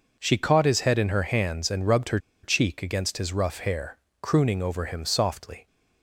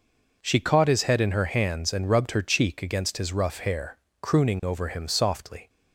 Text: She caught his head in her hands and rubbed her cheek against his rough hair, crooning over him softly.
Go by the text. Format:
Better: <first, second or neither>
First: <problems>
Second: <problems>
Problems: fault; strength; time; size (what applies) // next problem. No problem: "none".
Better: second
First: pauses between "her" and "cheek"; slight; at 2.1 s; 0.25 s long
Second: none